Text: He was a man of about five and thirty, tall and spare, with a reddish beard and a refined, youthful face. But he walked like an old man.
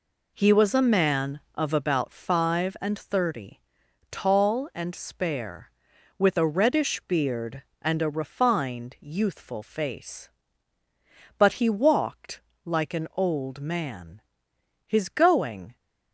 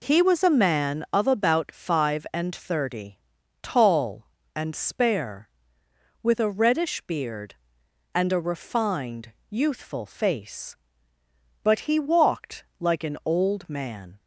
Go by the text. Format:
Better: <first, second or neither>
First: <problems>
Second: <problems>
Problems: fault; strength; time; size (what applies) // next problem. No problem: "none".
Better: second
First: pauses between "walked" and "like"; slight; at 12.4 s; 0.24 s long // goes on to say "His going"; noticeable; from 14.8 s on; 0.88 s long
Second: pauses between "walked" and "like"; slight; at 12.6 s; 0.16 s long